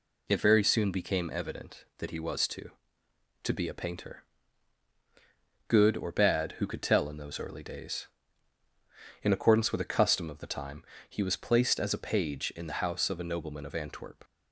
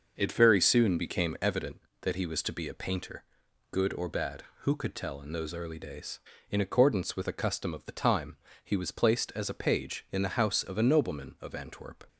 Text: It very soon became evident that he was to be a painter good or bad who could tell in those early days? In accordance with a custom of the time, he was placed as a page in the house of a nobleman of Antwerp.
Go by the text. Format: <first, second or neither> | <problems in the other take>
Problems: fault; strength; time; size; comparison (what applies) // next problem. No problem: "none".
second | says "to" twice; at 3.4 s // pauses between "painter" and "good"; strong; at 4.2 s; 1.4 s long; noticeable in the second